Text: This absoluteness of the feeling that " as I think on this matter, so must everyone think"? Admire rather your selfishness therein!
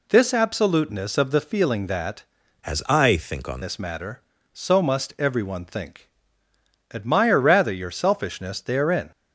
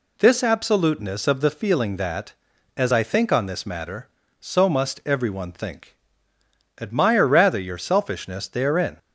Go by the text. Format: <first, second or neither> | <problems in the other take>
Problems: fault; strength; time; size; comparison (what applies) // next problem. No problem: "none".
second | changes voice from "as" to "on"; from 2.6 to 3.6 s; 1.0 s long